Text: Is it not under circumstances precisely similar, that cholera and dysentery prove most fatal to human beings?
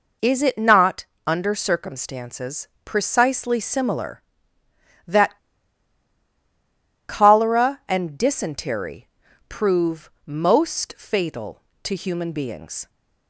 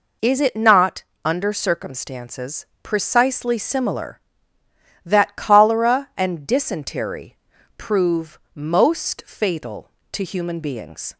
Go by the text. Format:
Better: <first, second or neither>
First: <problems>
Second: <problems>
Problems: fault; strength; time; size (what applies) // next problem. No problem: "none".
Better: second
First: pauses between "not" and "under"; slight; at 1.0 s; 0.20 s long // pauses between "circumstances" and "precisely"; slight; at 2.6 s; 0.16 s long // pauses between "that" and "cholera"; strong; at 5.3 s; 1.7 s long // pauses between "dysentery" and "prove"; at 9.0 s; 0.42 s long // pauses between "prove" and "most"; slight; at 10.1 s; 0.16 s long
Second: pauses between "not" and "under"; slight; at 1.0 s; 0.20 s long // pauses between "circumstances" and "precisely"; slight; at 2.6 s; 0.16 s long // pauses between "dysentery" and "prove"; at 7.3 s; 0.42 s long // pauses between "prove" and "most"; slight; at 8.3 s; 0.16 s long